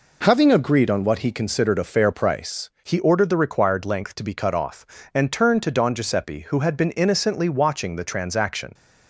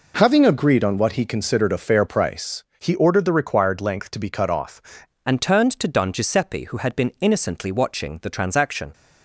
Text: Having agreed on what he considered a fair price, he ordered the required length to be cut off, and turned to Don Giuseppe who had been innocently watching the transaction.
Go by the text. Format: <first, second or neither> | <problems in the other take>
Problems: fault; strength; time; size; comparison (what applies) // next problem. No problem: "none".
first | changes voice at "and"; from 5.2 s on; 3.7 s long